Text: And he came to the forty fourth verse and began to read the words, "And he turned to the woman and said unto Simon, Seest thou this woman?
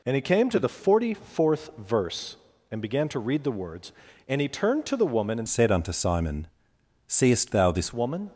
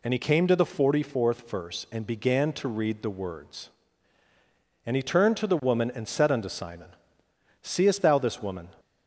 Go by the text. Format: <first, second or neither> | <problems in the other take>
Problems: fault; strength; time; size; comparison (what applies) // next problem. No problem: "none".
second | changes voice from "said" to "this"; from 5.4 to 7.9 s; 2.5 s long